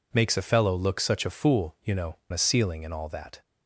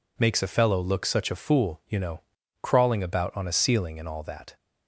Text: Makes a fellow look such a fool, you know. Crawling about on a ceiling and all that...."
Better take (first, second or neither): second